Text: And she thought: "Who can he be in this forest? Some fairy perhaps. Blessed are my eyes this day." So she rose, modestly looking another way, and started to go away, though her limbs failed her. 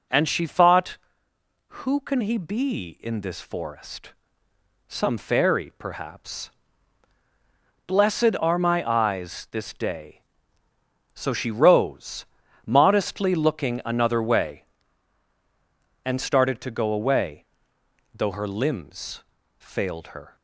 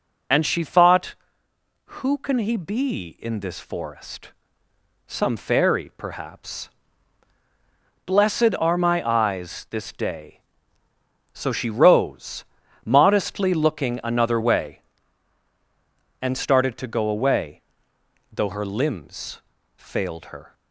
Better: first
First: pauses between "limbs" and "failed"; slight; at 19.2 s; 0.34 s long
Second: loses the start of "And"; at 0.3 s; 30 ms // pauses between "limbs" and "failed"; slight; at 19.4 s; 0.34 s long

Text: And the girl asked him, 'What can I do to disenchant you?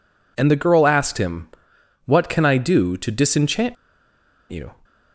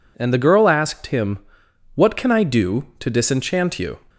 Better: second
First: pauses between "disenchant" and "you"; noticeable; at 3.7 s; 0.74 s long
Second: none

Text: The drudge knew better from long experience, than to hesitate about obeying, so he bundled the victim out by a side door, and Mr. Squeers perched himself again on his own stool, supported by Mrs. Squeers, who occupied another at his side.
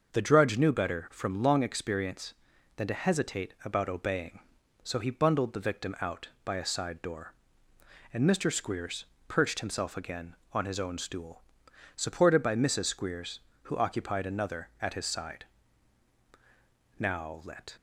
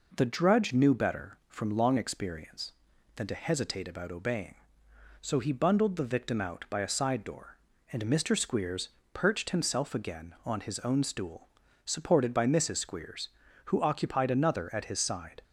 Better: second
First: starts louder than the rest; until 1.1 s; 6 dB // pauses between "Squeers" and "perched"; slight; at 9.0 s; 0.24 s long // goes on to say "Now let"; noticeable; from 16.9 s on; 0.76 s long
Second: pauses between "Squeers" and "perched"; slight; at 8.8 s; 0.26 s long

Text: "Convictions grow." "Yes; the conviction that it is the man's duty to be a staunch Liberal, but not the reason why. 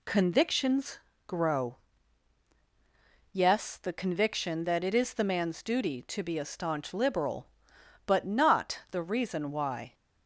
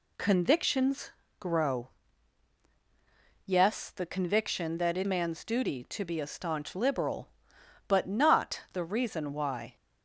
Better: first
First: pauses between "Convictions" and "grow"; slight; at 0.9 s; 0.30 s long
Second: pauses between "Convictions" and "grow"; slight; at 1.1 s; 0.30 s long // skips "is the"; at 5.0 s

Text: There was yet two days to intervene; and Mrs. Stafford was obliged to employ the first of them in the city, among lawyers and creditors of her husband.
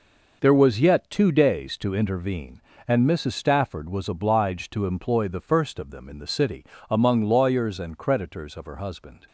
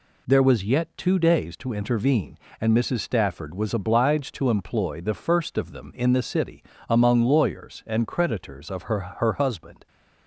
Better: first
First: none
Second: says "her" twice; at 8.9 s

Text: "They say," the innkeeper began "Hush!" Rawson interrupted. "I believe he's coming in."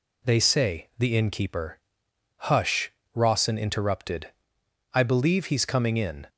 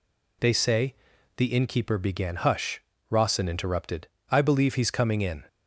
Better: second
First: skips "began"; at 2.1 s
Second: none

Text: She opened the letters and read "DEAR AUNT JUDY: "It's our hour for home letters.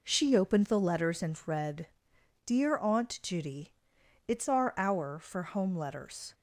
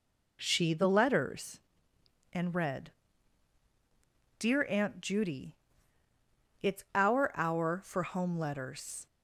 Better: first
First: pauses between "read" and "DEAR"; noticeable; at 1.8 s; 0.56 s long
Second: skips "opened"; at 0.7 s // pauses between "read" and "DEAR"; strong; at 2.9 s; 1.4 s long

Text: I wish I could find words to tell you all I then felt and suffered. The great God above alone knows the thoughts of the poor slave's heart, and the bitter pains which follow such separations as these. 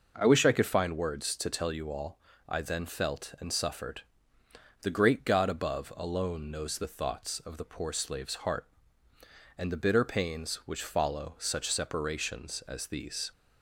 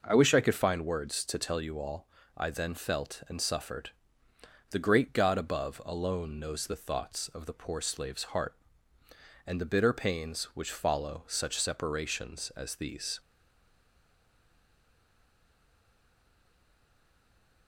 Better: first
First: pauses between "all" and "I"; slight; at 2.1 s; 0.30 s long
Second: pauses between "all" and "I"; slight; at 2.0 s; 0.30 s long // stays silent after the last word; strong; from 13.1 s on; 4.5 s long

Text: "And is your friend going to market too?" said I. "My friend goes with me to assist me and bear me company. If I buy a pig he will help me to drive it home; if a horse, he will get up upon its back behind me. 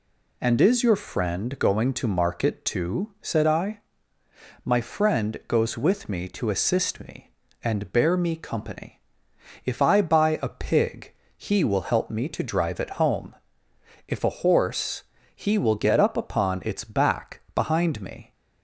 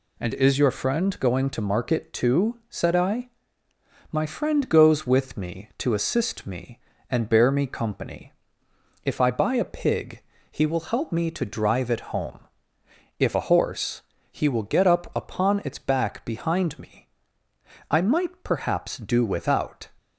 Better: first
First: pauses between "pig" and "he"; slight; at 11.1 s; 0.24 s long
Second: pauses between "pig" and "he"; slight; at 10.2 s; 0.28 s long // goes on to say "I might perhaps do without"; strong; from 17.8 s on; 1.9 s long

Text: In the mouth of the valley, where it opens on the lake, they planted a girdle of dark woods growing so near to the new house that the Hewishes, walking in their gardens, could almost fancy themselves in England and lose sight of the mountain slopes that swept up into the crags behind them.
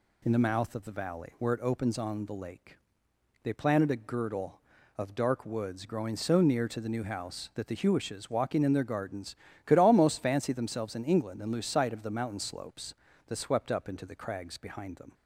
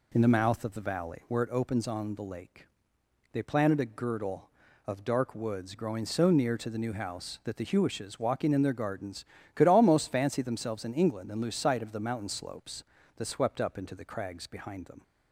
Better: first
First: none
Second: starts louder than the rest; until 1.2 s; 3.5 dB

